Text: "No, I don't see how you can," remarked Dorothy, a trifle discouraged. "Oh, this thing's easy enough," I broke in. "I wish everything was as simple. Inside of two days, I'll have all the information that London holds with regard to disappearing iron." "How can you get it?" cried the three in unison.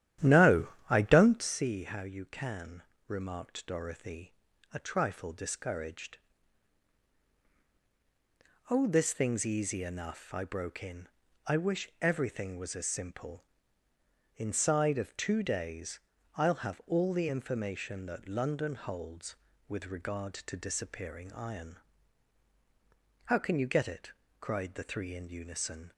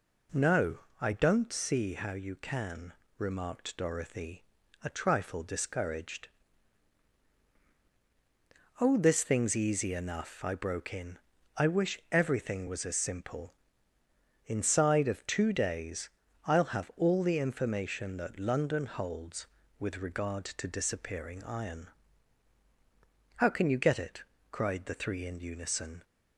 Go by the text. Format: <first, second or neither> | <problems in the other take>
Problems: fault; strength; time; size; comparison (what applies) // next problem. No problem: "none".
second | starts louder than the rest; strong; until 1.6 s; 11.5 dB